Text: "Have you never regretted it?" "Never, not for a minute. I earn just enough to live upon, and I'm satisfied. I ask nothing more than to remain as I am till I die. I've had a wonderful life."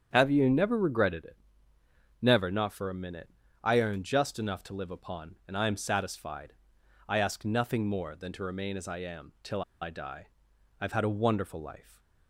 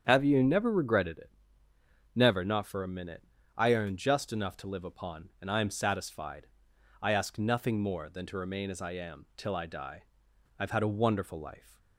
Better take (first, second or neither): second